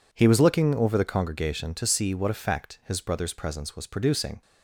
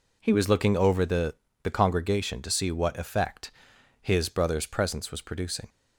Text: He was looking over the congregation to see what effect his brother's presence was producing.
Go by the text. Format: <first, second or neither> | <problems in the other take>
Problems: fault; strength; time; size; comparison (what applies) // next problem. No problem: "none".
first | says "the" twice; at 1.6 s // pauses between "effect" and "his"; noticeable; at 3.5 s; 0.50 s long